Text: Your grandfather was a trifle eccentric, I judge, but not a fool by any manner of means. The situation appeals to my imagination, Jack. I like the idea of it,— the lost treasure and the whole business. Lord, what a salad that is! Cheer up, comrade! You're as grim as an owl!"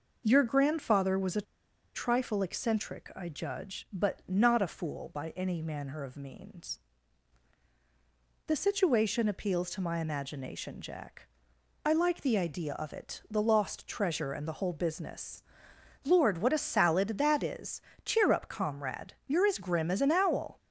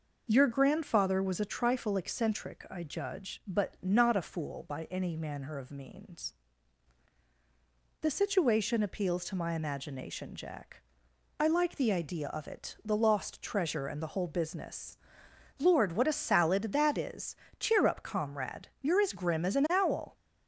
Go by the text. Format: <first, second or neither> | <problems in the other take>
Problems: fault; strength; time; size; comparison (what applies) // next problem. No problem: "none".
second | pauses between "a" and "trifle"; noticeable; at 1.4 s; 0.52 s long